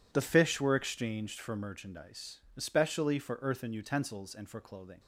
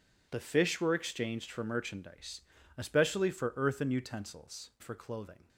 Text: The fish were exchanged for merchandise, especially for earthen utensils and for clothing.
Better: first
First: none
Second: skips "and"; at 4.7 s

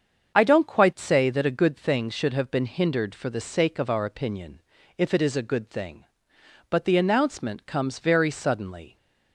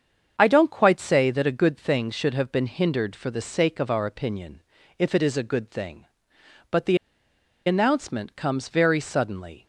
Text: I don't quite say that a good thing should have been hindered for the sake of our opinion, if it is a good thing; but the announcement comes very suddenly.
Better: first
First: starts louder than the rest; strong; until 1.4 s; 7 dB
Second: starts louder than the rest; strong; until 1.3 s; 7 dB // pauses between "the" and "announcement"; noticeable; at 6.9 s; 0.69 s long

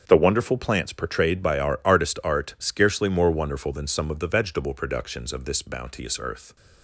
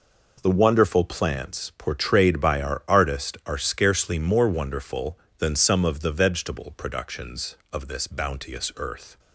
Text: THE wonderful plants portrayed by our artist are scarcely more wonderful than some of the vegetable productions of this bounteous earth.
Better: second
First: starts louder than the rest; until 1.0 s; 7 dB // says "art" for "are"; at 2.2 s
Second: none

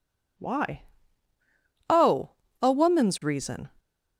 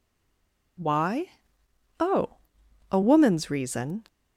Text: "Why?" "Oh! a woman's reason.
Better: first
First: none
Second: stays silent before the first word; slight; until 0.7 s; 0.7 s long

